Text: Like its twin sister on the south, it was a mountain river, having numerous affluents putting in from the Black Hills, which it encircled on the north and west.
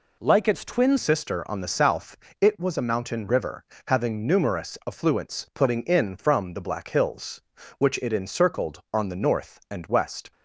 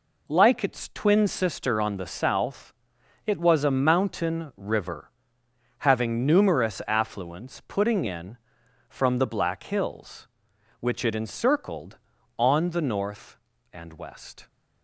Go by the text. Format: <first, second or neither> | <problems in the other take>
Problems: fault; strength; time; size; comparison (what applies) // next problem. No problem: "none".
second | changes voice at "sister"; from 0.9 s on; 9.4 s long